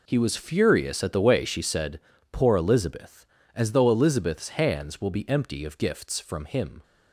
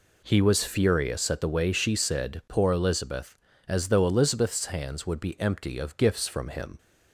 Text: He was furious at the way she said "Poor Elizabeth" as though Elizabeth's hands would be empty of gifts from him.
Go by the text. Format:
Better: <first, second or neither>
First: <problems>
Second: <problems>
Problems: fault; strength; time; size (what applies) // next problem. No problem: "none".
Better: second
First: pauses between "said" and "Poor"; slight; at 1.9 s; 0.32 s long // says "will" for "would"; at 5.0 s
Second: none